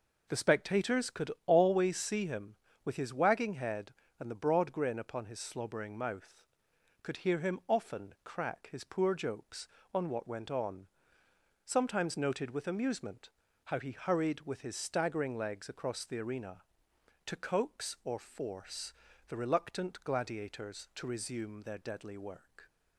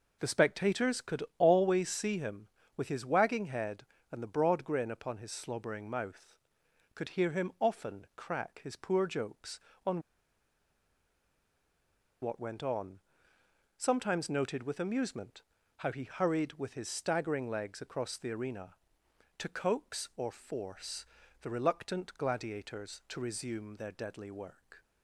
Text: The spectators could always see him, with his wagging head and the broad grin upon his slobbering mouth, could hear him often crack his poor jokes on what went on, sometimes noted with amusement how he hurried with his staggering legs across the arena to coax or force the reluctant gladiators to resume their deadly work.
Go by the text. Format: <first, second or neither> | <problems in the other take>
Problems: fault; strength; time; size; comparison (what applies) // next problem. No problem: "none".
first | pauses between "could" and "always"; slight; at 1.2 s; 0.16 s long; slight in the first // pauses between "on" and "what"; strong; at 10.0 s; 2.2 s long // pauses between "amusement" and "how"; slight; at 15.4 s; 0.36 s long; slight in the first // pauses between "force" and "the"; slight; at 21.0 s; 0.36 s long; slight in the first